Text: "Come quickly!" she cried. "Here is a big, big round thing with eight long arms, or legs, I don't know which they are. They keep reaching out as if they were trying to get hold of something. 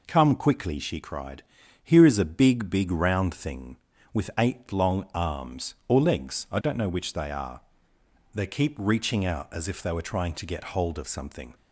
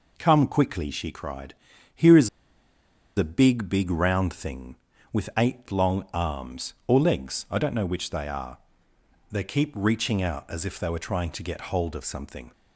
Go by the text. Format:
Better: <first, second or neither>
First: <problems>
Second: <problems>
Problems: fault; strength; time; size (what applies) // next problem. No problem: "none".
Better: first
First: none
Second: pauses between "is" and "a"; noticeable; at 2.2 s; 0.88 s long